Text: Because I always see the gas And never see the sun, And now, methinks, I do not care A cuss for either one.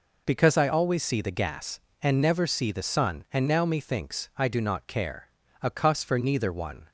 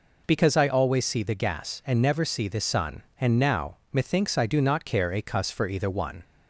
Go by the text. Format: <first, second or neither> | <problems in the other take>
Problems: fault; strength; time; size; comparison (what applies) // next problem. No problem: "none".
second | pauses between "care" and "A"; slight; at 5.2 s; 0.34 s long // says "neither" for "either"; at 6.1 s